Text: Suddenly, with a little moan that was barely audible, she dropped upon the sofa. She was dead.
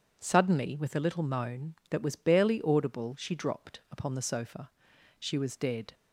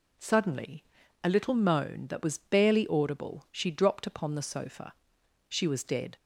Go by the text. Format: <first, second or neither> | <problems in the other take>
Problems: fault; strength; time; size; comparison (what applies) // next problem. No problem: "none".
first | skips "with"; at 1.0 s